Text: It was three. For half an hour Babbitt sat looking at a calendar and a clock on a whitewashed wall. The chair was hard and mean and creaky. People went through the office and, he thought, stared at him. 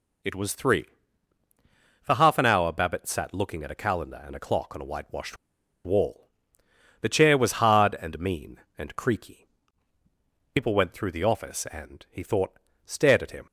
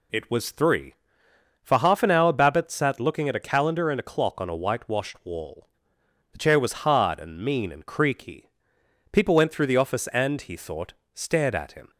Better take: second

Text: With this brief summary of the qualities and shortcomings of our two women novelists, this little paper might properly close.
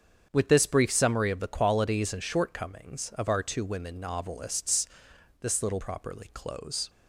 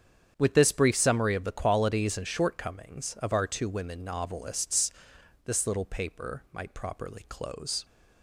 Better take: second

